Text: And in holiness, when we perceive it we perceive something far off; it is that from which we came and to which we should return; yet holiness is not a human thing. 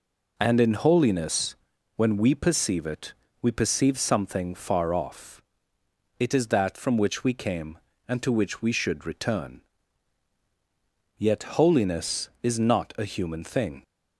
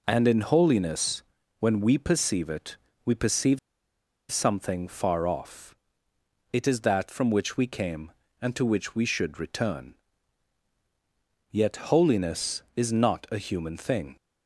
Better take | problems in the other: first | pauses between "it" and "we"; slight; at 2.7 s; 0.30 s long; slight in the first // pauses between "perceive" and "something"; noticeable; at 3.5 s; 0.72 s long

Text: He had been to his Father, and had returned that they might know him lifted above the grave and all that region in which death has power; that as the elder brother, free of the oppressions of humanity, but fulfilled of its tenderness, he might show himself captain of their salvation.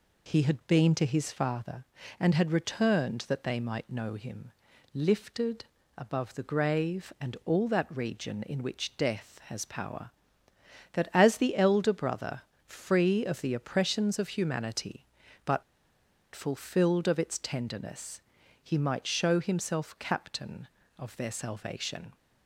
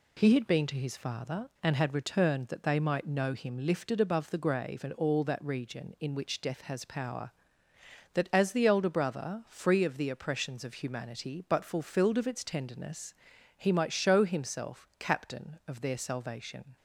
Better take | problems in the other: second | pauses between "him" and "lifted"; at 4.5 s; 0.42 s long // pauses between "lifted" and "above"; slight; at 5.6 s; 0.34 s long // pauses between "but" and "fulfilled"; noticeable; at 15.6 s; 0.71 s long

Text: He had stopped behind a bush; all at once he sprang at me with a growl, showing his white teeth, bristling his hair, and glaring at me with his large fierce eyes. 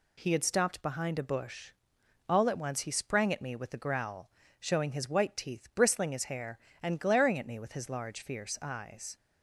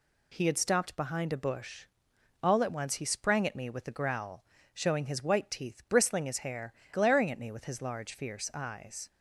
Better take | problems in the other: first | skips "and"; at 6.8 s

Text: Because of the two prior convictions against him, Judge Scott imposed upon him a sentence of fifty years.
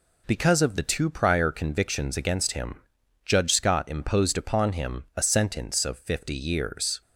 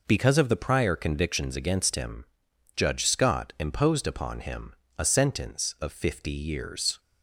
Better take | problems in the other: first | skips "two"; at 0.5 s // pauses between "him" and "a"; slight; at 4.7 s; 0.24 s long

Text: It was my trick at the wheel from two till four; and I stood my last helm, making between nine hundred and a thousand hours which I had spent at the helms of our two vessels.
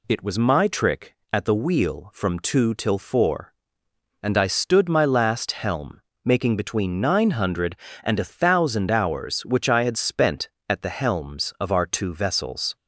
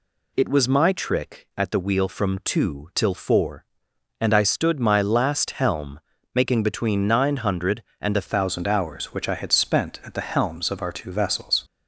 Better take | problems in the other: first | changes voice at "thousand"; from 8.2 s on; 3.4 s long

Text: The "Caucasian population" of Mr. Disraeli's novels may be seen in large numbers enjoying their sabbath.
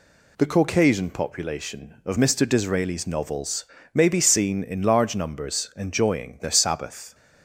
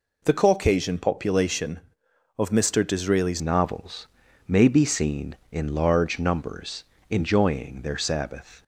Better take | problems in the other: first | changes voice at "novels"; from 3.4 s on; 5.2 s long // pauses between "novels" and "may"; at 4.0 s; 0.40 s long; slight in the first // pauses between "numbers" and "enjoying"; slight; at 6.8 s; 0.24 s long

